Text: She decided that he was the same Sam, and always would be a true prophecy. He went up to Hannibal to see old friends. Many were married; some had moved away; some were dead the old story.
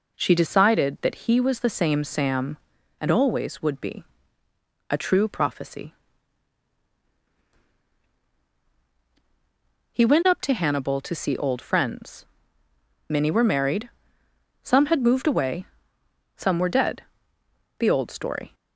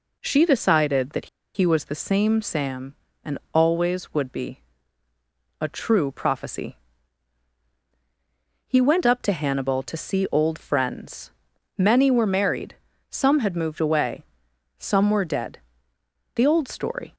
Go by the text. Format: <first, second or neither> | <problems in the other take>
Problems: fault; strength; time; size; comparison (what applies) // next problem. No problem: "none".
first | pauses between "that" and "he"; slight; at 1.2 s; 0.28 s long // pauses between "and" and "always"; slight; at 3.3 s; 0.16 s long // pauses between "be" and "a"; at 4.6 s; 1.0 s long; noticeable in the first // pauses between "dead" and "the"; noticeable; at 15.6 s; 0.74 s long; noticeable in the first